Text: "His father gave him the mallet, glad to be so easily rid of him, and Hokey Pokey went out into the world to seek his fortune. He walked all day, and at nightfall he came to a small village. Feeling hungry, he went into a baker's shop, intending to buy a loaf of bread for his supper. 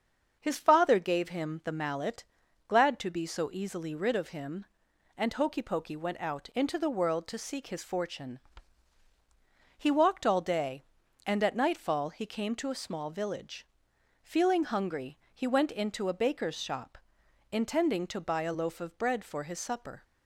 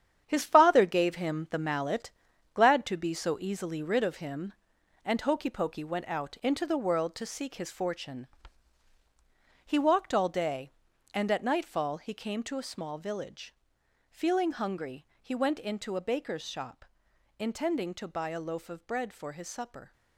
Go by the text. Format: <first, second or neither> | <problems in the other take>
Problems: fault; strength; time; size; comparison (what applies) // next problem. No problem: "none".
first | gets quieter; strong; throughout; 9 dB // starts louder than the rest; strong; until 1.2 s; 9 dB; also in the first